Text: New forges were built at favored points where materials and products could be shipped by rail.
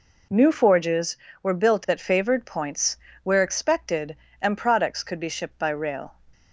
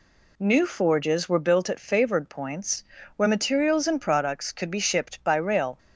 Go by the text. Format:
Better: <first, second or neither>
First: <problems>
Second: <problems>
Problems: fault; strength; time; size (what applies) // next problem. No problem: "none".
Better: second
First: pauses between "points" and "where"; slight; at 2.9 s; 0.26 s long // says "expected" for "materials"; at 3.4 s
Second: pauses between "points" and "where"; slight; at 2.8 s; 0.32 s long